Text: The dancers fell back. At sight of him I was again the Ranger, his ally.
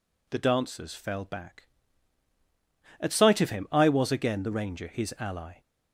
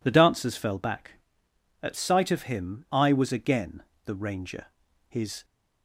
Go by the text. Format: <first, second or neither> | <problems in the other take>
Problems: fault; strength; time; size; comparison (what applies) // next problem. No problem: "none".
first | pauses between "again" and "the"; slight; at 3.8 s; 0.21 s long // stops before "ally"; at 5.4 s